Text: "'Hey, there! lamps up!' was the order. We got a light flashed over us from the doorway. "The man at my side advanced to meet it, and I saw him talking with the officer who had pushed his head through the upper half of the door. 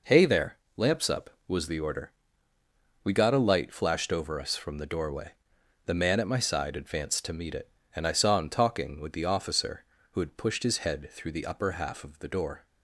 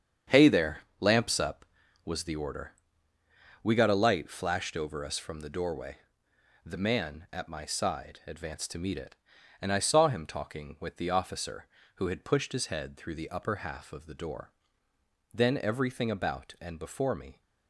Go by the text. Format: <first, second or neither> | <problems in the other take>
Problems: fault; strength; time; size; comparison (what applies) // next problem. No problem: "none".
first | starts louder than the rest; strong; until 1.5 s; 8 dB // goes on to say "Then everything about and before me"; strong; from 15.3 s on; 2.0 s long